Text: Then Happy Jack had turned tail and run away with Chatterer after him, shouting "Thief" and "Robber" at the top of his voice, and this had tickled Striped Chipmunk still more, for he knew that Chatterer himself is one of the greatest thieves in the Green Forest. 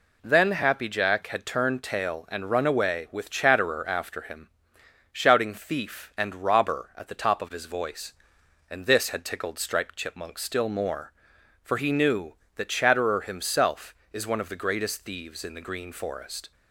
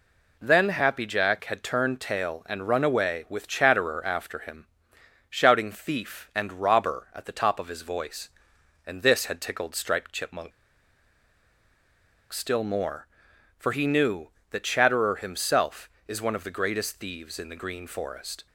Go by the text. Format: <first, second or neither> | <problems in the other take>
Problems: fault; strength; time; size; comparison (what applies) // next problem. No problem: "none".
first | pauses between "Chipmunk" and "still"; strong; at 10.5 s; 1.8 s long